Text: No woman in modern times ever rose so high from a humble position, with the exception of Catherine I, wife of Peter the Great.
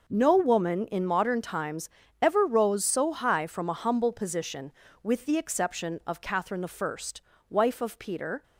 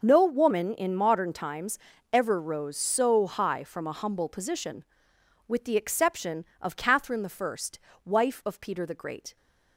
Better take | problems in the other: second | pauses between "times" and "ever"; slight; at 1.8 s; 0.34 s long; slight in the second // stops before "the Great"; at 8.4 s

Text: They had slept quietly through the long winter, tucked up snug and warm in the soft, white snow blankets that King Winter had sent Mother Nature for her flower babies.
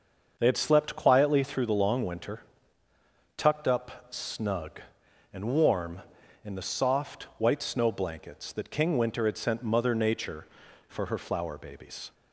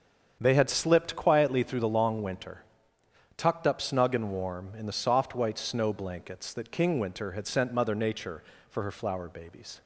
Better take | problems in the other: first | starts louder than the rest; strong; until 1.4 s; 7.5 dB; also in the first // says "slipped" for "slept"; at 0.6 s

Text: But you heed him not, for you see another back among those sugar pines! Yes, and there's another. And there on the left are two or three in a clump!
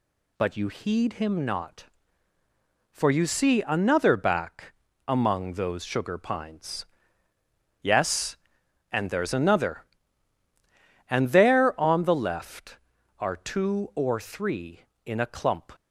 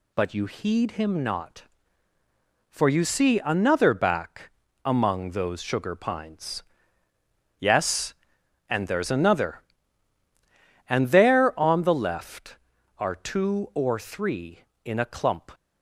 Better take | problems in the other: neither | pauses between "back" and "among"; slight; the same in both

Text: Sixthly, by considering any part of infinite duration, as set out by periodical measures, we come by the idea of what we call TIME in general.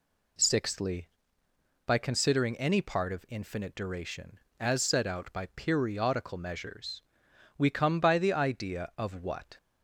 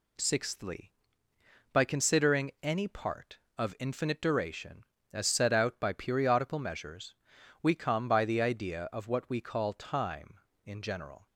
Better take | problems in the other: second | stops before "we call TIME in general"; at 9.5 s

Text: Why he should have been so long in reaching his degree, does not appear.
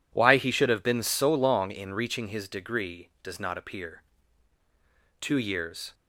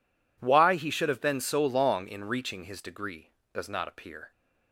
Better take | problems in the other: second | goes on to say "Two years"; noticeable; from 5.2 s on; 0.72 s long

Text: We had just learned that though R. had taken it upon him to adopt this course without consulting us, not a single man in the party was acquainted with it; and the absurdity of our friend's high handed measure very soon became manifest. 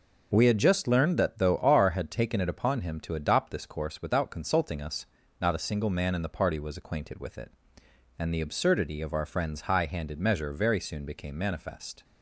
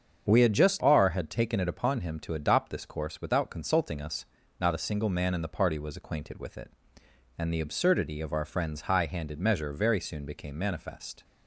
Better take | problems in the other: first | starts louder than the rest; until 1.2 s; 7 dB // skips "learned that though"; at 0.8 s

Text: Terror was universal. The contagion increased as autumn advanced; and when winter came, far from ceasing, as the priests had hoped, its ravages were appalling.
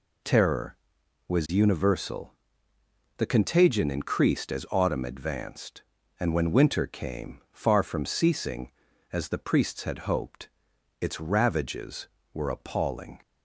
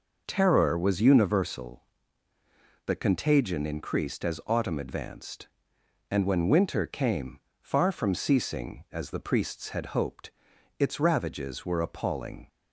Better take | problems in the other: neither | none

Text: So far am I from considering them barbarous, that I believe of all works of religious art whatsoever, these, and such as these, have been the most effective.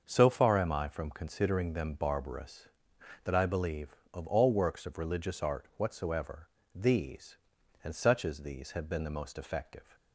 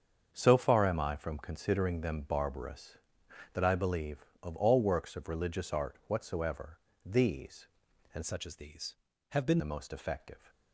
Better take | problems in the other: first | starts louder than the rest; strong; until 1.3 s; 7 dB; also in the first // changes voice from "such" to "been"; from 8.2 to 9.5 s; 1.3 s long

